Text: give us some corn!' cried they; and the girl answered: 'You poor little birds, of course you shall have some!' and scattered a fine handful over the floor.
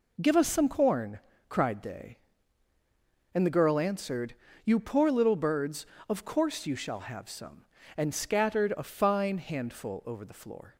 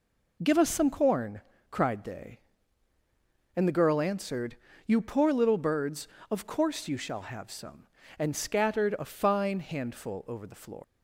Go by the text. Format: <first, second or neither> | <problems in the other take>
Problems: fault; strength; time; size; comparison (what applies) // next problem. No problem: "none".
first | leaves "floor" unfinished; at 10.8 s; 130 ms